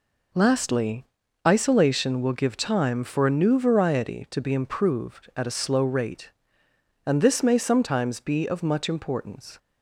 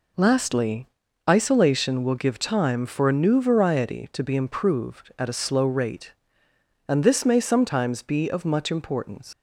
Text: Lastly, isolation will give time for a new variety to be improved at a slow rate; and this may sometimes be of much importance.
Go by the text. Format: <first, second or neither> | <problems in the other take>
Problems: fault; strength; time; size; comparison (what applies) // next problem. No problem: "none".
first | leaves "importance" unfinished; at 9.3 s; 70 ms